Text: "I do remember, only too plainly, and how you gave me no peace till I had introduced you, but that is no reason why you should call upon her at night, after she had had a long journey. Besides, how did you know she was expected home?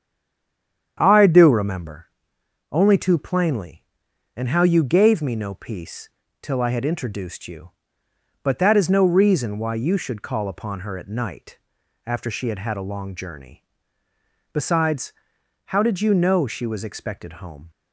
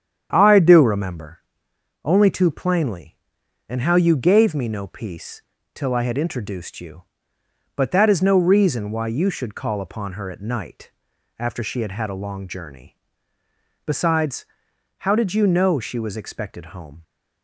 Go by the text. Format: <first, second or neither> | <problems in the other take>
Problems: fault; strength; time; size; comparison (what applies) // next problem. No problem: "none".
second | stays silent before the first word; slight; until 0.9 s; 0.9 s long // starts louder than the rest; strong; until 2.0 s; 8.5 dB; strong in the second // pauses between "peace" and "till"; slight; at 6.0 s; 0.32 s long; slight in the second